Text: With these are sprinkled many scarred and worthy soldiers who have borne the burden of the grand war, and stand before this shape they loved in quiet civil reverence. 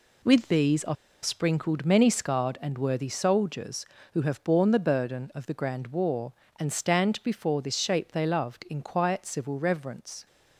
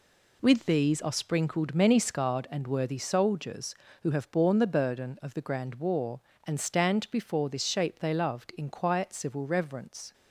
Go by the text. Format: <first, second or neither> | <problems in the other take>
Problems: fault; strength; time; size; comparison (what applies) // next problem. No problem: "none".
second | pauses between "are" and "sprinkled"; slight; at 0.9 s; 0.28 s long